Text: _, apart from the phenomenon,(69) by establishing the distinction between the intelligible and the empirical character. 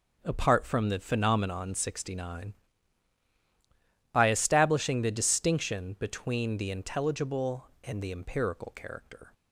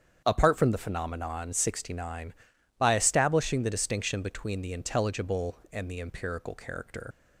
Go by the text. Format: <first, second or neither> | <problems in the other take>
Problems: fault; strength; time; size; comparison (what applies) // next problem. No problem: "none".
first | starts louder than the rest; strong; until 1.2 s; 8 dB // leaves "character" unfinished; at 7.1 s; 70 ms